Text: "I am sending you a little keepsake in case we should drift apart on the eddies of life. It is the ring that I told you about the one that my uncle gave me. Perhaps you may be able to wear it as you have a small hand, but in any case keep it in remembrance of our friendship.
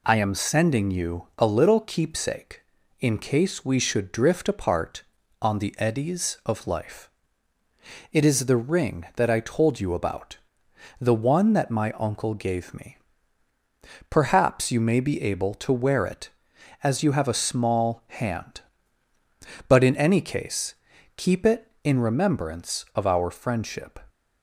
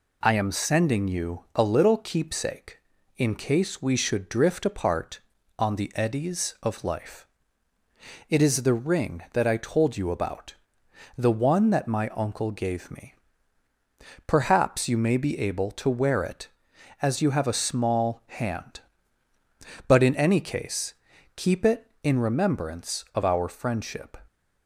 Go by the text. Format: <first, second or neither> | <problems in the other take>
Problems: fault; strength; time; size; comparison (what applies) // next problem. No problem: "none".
neither | pauses between "about" and "the"; noticeable; the same in both // pauses between "case" and "keep"; the same in both